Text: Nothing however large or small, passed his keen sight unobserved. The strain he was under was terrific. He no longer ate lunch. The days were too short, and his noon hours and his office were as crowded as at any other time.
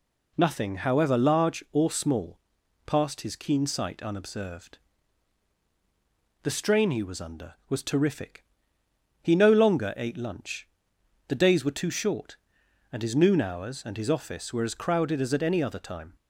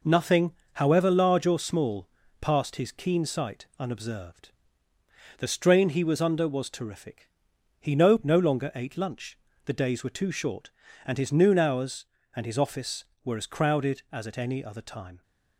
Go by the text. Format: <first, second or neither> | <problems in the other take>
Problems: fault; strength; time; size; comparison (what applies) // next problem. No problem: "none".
first | pauses between "Nothing" and "however"; slight; at 0.5 s; 0.22 s long // says "no" twice; at 8.2 s